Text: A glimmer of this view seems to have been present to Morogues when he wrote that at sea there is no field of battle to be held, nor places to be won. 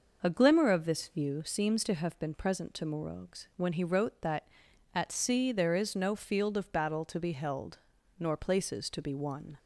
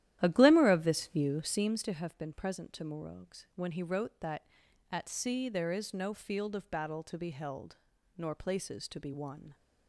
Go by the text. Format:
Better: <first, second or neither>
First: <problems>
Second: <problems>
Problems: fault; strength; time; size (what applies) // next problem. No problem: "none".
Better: first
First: none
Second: starts louder than the rest; strong; until 1.8 s; 12.5 dB